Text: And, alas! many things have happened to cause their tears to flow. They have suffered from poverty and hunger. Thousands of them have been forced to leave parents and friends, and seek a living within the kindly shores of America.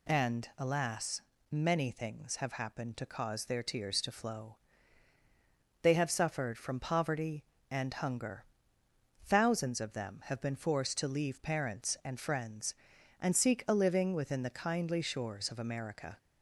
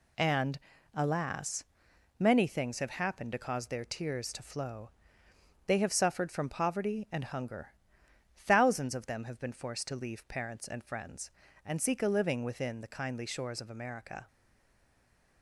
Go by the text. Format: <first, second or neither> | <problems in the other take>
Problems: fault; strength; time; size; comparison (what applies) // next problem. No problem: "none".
first | stays silent after the last word; from 14.2 s on; 1.2 s long